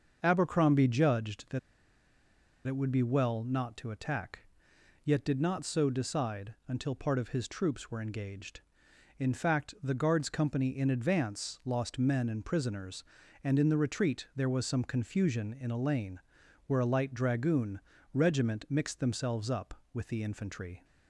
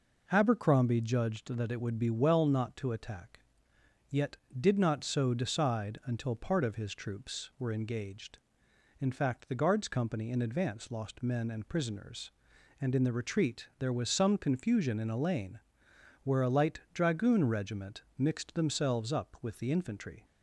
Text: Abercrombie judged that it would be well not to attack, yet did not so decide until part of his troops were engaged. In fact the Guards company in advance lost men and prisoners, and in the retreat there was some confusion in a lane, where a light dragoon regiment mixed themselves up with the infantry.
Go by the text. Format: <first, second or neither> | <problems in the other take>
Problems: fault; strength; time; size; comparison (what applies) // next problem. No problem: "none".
second | starts louder than the rest; until 1.2 s; 6.5 dB // pauses between "that" and "it"; at 1.5 s; 1.0 s long // pauses between "dragoon" and "regiment"; slight; at 17.7 s; 0.34 s long